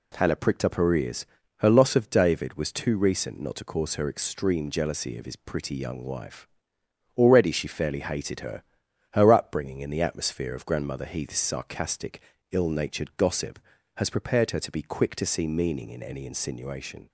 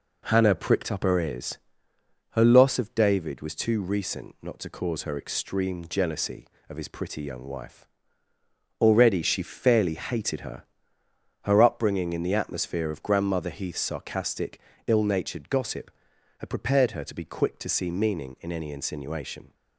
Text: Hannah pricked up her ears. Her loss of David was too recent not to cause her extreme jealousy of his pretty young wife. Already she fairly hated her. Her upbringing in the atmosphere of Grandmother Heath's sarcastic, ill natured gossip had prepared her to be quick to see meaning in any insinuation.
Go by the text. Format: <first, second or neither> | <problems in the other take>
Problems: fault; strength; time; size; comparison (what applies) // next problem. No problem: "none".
second | says "has" for "had"; at 13.9 s